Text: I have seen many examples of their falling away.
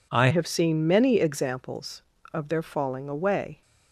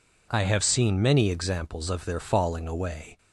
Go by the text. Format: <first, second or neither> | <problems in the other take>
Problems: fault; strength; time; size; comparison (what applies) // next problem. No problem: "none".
second | changes voice at "have"; from 0.3 s on; 3.3 s long